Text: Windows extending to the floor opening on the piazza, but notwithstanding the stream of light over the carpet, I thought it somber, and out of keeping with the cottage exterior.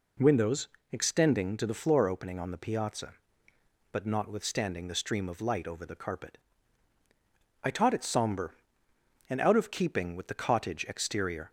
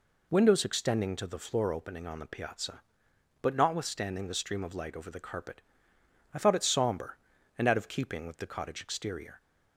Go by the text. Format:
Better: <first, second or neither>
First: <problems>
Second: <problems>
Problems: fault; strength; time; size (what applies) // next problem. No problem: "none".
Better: second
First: pauses between "Windows" and "extending"; slight; at 0.6 s; 0.24 s long // says "taught" for "thought"; at 7.6 s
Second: none